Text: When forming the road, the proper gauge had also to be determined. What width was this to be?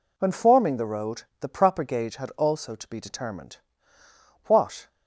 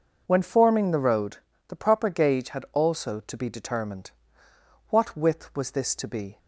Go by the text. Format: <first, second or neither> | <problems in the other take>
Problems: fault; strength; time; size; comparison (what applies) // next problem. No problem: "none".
second | stops before "width was this to be"; at 4.8 s